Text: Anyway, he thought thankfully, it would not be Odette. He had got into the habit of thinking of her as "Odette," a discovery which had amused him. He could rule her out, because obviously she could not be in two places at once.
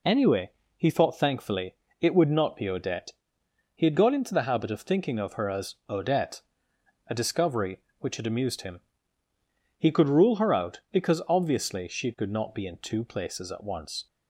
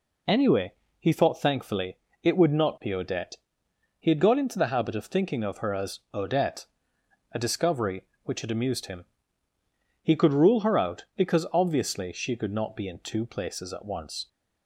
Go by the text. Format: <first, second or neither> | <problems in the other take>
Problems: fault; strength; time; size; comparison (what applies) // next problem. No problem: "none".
neither | none